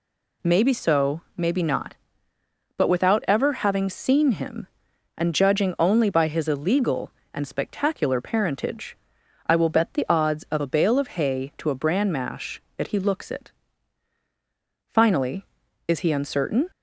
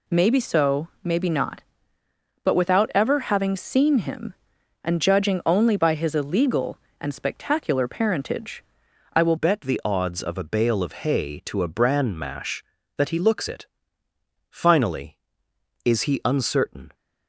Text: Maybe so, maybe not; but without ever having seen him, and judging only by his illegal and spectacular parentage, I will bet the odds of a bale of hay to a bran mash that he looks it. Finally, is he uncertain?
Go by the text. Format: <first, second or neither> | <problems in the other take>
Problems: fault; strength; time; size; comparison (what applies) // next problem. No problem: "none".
first | changes voice at "bet"; from 9.3 s on; 7.6 s long